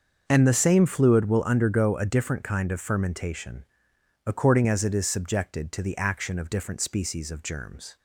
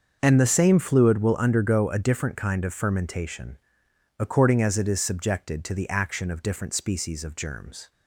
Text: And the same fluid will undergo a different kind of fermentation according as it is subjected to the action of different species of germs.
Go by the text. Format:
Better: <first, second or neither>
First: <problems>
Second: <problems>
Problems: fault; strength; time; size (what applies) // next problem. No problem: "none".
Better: neither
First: starts louder than the rest; until 1.2 s; 6.5 dB // pauses between "fermentation" and "according"; noticeable; at 3.6 s; 0.64 s long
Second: starts louder than the rest; until 1.2 s; 6.5 dB // pauses between "fermentation" and "according"; noticeable; at 3.5 s; 0.64 s long